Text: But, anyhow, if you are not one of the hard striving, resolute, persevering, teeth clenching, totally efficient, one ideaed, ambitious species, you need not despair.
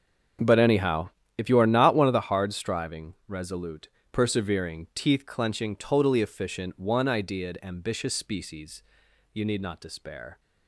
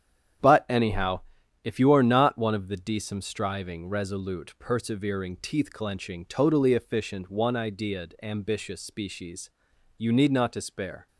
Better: first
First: starts louder than the rest; strong; until 1.6 s; 7 dB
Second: starts louder than the rest; strong; until 1.8 s; 9 dB // says "decem" for "hard"; at 2.7 s

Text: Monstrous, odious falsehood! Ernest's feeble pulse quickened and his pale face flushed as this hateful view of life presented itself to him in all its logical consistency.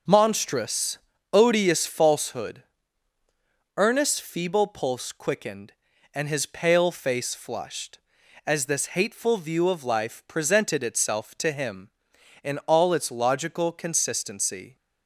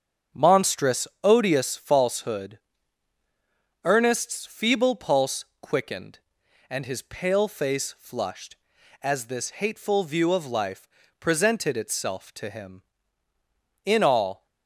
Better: first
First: starts louder than the rest; noticeable; until 1.4 s; 6 dB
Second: starts louder than the rest; strong; until 1.5 s; 7.5 dB // pauses between "pulse" and "quickened"; slight; at 5.4 s; 0.16 s long // pauses between "life" and "presented"; slight; at 10.8 s; 0.32 s long // stops before "its logical consistency"; at 14.4 s

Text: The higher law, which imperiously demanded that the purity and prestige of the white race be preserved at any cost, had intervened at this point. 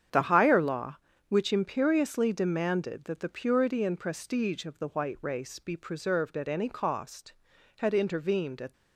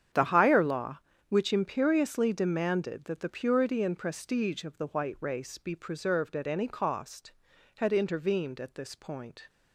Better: second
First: starts louder than the rest; strong; until 1.4 s; 8.5 dB // stops before "this point"; at 8.7 s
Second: starts louder than the rest; strong; until 1.4 s; 8.5 dB

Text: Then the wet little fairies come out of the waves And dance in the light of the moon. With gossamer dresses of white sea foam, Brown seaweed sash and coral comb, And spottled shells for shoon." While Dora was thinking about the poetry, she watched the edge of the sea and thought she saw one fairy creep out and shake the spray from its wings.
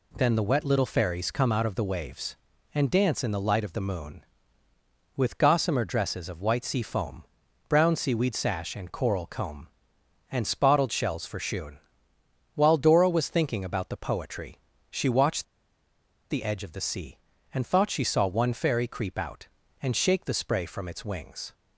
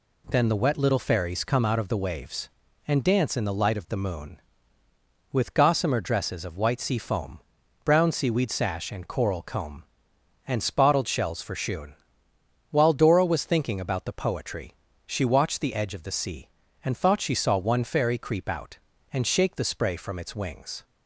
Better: second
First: pauses between "watched" and "the"; noticeable; at 15.4 s; 0.86 s long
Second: none

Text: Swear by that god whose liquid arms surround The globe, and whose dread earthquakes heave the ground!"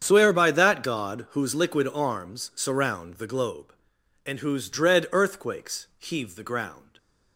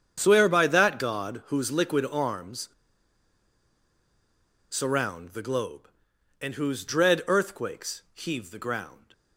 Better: first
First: starts louder than the rest; strong; until 1.0 s; 8 dB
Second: starts louder than the rest; strong; until 1.2 s; 8 dB // pauses between "arms" and "surround"; strong; at 2.6 s; 2.0 s long

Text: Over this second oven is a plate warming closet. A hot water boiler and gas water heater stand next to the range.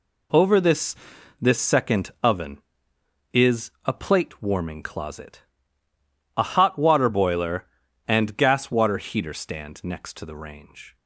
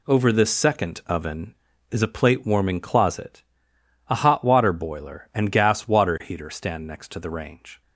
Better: second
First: says "this" twice; at 1.4 s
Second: none

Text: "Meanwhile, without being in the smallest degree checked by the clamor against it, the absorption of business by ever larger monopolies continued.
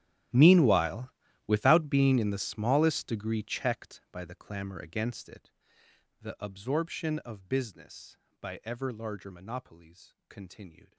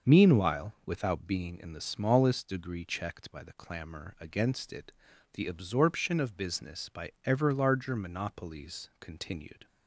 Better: second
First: gets quieter; strong; throughout; 20.5 dB // starts louder than the rest; strong; until 1.6 s; 11 dB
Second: starts louder than the rest; until 1.1 s; 6.5 dB

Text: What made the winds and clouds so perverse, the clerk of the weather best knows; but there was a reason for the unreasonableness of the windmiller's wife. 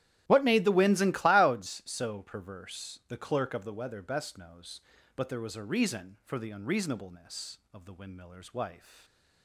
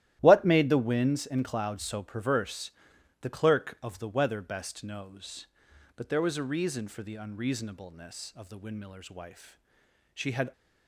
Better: first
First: starts louder than the rest; strong; until 1.2 s; 12.5 dB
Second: starts louder than the rest; strong; until 1.2 s; 13.5 dB // goes on to say "She had"; slight; from 10.1 s on; 0.40 s long

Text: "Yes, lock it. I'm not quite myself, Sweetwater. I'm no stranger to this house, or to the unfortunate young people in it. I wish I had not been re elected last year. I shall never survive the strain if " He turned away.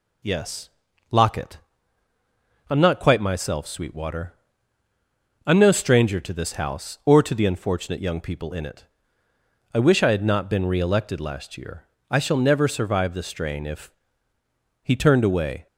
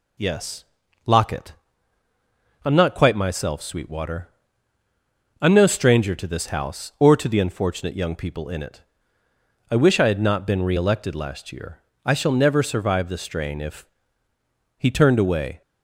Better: neither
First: none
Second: none

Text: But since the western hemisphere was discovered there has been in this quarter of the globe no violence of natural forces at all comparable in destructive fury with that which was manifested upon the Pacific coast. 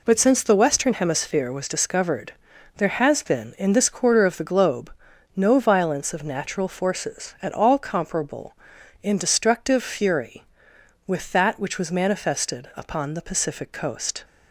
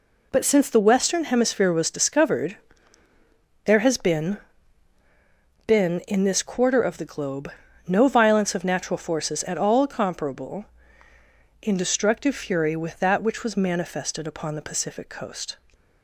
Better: first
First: pauses between "discovered" and "there"; at 2.3 s; 0.44 s long // pauses between "globe" and "no"; at 4.9 s; 0.44 s long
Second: pauses between "discovered" and "there"; at 2.5 s; 1.1 s long // says "been" twice; at 5.6 s // pauses between "globe" and "no"; at 7.4 s; 0.38 s long

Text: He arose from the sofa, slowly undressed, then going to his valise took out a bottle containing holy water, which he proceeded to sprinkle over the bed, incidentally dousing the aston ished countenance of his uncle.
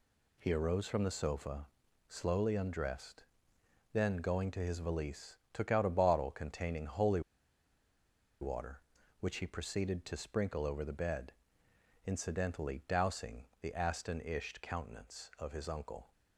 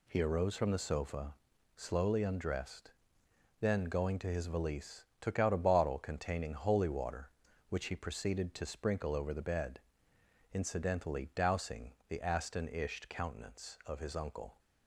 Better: second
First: pauses between "valise" and "took"; slight; at 5.3 s; 0.16 s long // pauses between "holy" and "water"; at 7.2 s; 1.2 s long // pauses between "dousing" and "the"; slight; at 13.4 s; 0.16 s long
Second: pauses between "valise" and "took"; slight; at 5.0 s; 0.16 s long // pauses between "dousing" and "the"; slight; at 11.9 s; 0.16 s long

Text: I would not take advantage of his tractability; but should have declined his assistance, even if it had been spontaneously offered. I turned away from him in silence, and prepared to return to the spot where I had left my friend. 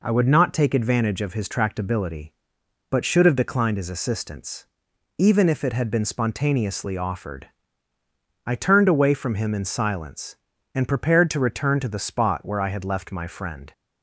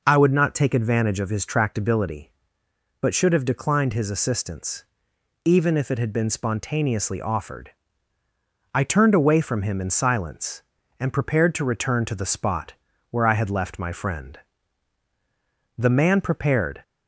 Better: first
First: none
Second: pauses between "spot" and "where"; at 12.7 s; 0.38 s long // goes on to say "The man prepared"; noticeable; from 15.7 s on; 1.0 s long

